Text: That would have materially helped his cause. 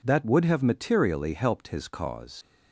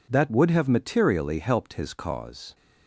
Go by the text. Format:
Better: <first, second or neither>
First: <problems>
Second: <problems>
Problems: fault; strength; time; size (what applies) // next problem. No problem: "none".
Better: second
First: leaves "cause" unfinished; at 2.4 s; 80 ms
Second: none